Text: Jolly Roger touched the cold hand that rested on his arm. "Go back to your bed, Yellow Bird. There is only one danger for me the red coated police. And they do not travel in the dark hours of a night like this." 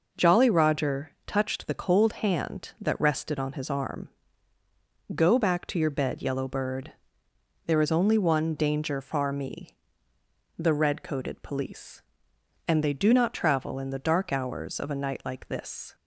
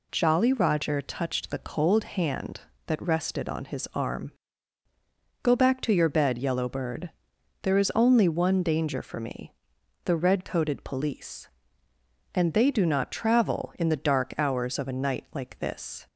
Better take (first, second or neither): second